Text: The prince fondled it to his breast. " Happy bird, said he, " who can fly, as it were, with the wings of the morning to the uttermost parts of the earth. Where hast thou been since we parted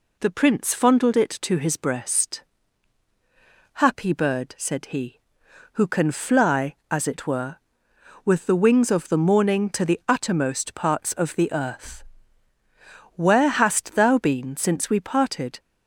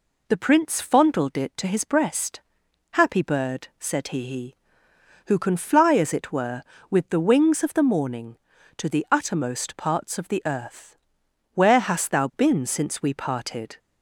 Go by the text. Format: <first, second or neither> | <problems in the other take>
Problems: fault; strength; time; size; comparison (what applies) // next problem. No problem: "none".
first | says "he" twice; at 4.2 s